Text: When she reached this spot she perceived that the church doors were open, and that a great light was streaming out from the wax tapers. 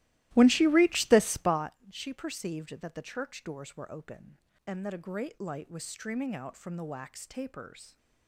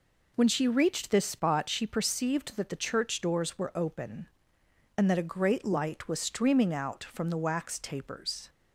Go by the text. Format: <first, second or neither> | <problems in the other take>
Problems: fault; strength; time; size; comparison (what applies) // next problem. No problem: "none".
second | starts louder than the rest; strong; until 1.7 s; 16.5 dB // pauses between "spot" and "she"; slight; at 1.7 s; 0.16 s long